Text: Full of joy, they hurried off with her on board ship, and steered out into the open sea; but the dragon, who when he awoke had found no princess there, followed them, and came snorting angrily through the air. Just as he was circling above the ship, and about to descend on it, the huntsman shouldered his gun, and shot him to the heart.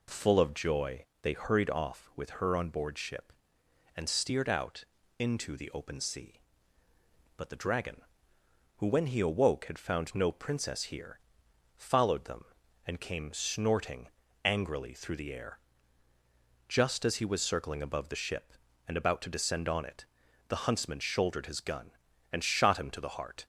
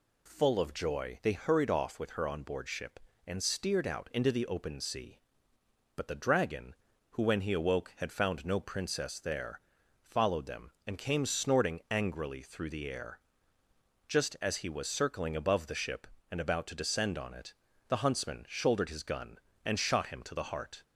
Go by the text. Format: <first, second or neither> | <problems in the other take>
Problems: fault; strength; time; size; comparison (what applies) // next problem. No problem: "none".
second | pauses between "out" and "into"; slight; at 4.8 s; 0.34 s long // says "here" for "there"; at 10.8 s // pauses between "snorting" and "angrily"; slight; at 14.0 s; 0.34 s long